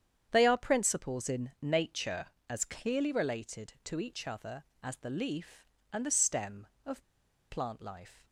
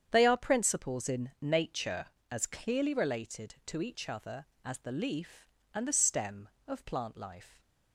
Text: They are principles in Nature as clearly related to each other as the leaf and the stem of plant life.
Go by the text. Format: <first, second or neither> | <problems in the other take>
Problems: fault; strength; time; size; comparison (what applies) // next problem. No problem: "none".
second | starts louder than the rest; strong; until 1.3 s; 8.5 dB; strong in the second // pauses between "of" and "plant"; noticeable; at 7.0 s; 0.47 s long